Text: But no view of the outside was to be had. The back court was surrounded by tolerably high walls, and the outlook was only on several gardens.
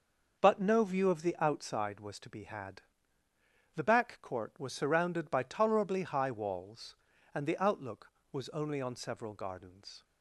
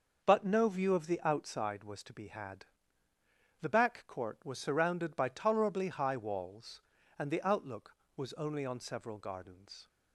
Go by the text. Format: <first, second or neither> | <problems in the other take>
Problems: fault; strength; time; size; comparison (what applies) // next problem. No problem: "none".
neither | starts louder than the rest; the same in both